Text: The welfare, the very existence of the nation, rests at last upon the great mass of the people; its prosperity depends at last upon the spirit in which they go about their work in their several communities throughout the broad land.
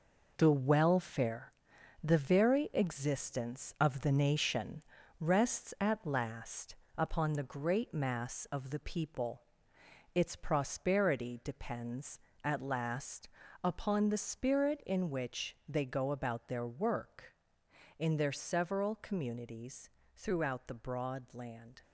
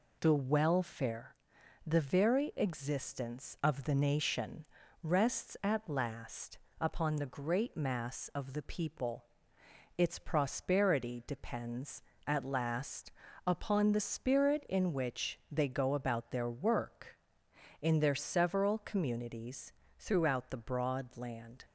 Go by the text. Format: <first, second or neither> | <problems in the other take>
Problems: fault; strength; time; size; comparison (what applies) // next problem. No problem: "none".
second | gets quieter; strong; throughout; 7.5 dB // pauses between "last" and "upon"; slight; at 6.7 s; 0.24 s long; slight in the second // pauses between "last" and "upon"; slight; at 13.2 s; 0.34 s long; slight in the second // pauses between "communities" and "throughout"; slight; at 19.8 s; 0.26 s long; slight in the second